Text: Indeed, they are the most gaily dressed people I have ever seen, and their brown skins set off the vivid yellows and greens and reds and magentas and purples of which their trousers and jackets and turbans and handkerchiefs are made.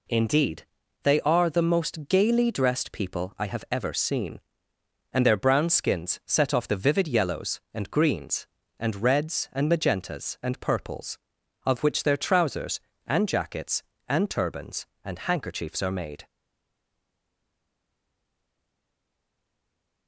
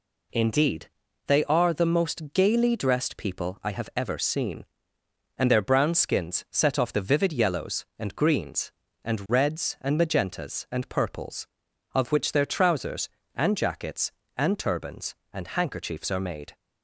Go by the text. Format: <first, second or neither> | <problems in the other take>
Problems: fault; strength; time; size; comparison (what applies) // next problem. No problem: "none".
second | stays silent after the last word; strong; from 16.2 s on; 3.8 s long